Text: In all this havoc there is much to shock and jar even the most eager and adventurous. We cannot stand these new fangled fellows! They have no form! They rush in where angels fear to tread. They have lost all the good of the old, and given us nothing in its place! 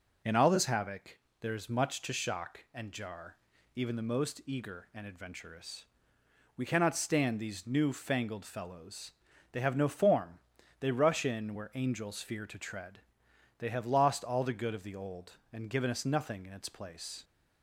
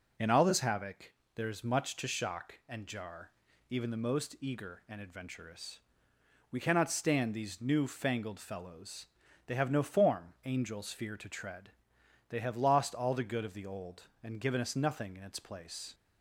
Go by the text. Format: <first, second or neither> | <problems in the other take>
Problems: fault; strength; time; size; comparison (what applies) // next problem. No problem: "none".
first | pauses between "havoc" and "there"; slight; at 1.1 s; 0.22 s long; slight in the first // pauses between "jar" and "even"; at 3.3 s; 0.38 s long; also in the first // skips "They rush in where"; at 10.3 s